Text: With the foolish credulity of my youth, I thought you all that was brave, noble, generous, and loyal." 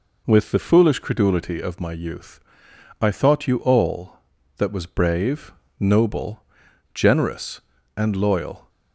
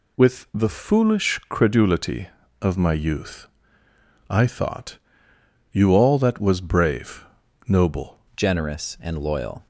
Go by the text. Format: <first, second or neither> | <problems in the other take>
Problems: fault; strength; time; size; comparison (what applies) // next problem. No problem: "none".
first | pauses between "thought" and "you"; noticeable; at 4.9 s; 0.76 s long // changes voice at "generous"; from 8.3 s on; 1.3 s long